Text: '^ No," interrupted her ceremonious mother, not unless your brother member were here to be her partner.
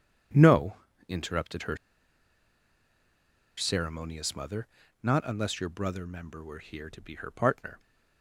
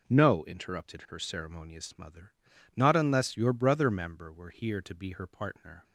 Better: second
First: starts louder than the rest; strong; until 1.6 s; 8.5 dB // pauses between "her" and "ceremonious"; strong; at 1.7 s; 1.8 s long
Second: none

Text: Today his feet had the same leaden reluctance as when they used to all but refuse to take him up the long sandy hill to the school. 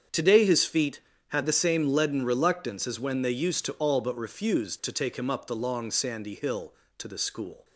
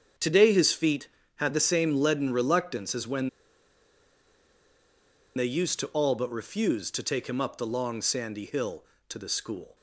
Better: first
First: starts louder than the rest; strong; until 1.3 s; 7.5 dB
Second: starts louder than the rest; strong; until 1.4 s; 7.5 dB // pauses between "when" and "they"; strong; at 3.2 s; 2.0 s long

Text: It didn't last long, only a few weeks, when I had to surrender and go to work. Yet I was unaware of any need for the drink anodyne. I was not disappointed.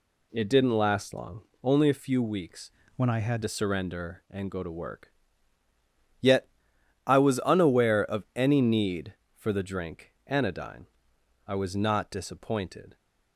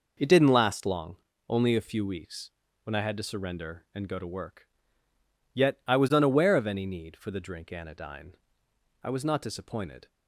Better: second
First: changes voice from "when" to "had"; from 2.9 to 3.4 s; 0.5 s long // pauses between "Yet" and "I"; noticeable; at 6.4 s; 0.58 s long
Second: none

